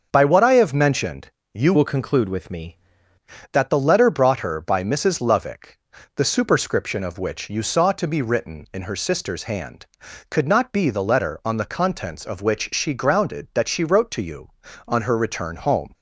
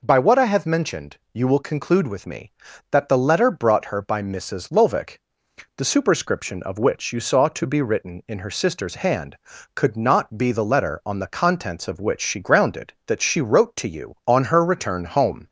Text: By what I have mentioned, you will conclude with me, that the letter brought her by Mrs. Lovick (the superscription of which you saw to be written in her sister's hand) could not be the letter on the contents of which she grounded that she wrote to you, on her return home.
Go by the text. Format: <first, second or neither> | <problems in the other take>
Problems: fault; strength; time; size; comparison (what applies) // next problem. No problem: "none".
second | starts louder than the rest; until 1.1 s; 6.5 dB // changes voice from "will" to "me"; from 1.7 to 2.7 s; 1.0 s long